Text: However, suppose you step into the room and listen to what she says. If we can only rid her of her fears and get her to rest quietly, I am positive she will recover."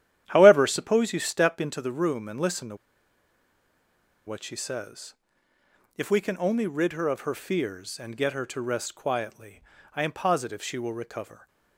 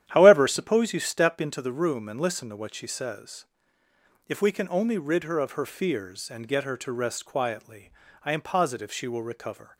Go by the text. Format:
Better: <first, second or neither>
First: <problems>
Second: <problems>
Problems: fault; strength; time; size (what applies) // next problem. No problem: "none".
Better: second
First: starts louder than the rest; strong; until 1.2 s; 11 dB // pauses between "to" and "what"; strong; at 2.7 s; 1.5 s long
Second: starts louder than the rest; strong; until 1.1 s; 11 dB